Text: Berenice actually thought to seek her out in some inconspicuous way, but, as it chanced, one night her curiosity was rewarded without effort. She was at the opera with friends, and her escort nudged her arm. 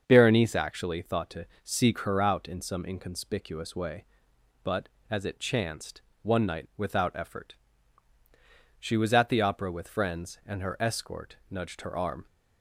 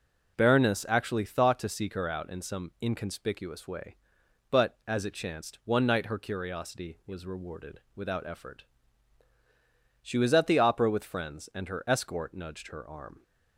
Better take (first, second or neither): second